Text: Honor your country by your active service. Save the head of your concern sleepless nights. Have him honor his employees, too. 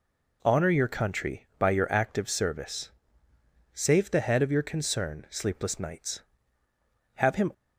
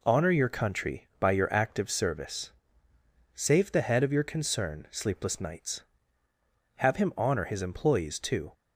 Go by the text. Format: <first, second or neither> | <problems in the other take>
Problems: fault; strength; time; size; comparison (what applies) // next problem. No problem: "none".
second | stops before "honor his employees too"; at 7.5 s